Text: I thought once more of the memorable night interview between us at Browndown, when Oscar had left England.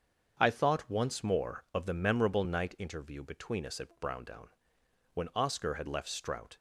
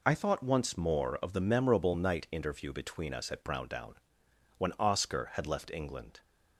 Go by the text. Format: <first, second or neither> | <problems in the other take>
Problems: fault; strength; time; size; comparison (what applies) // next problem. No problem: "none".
second | starts louder than the rest; until 1.3 s; 7 dB // says "Strout" for "England"; at 6.0 s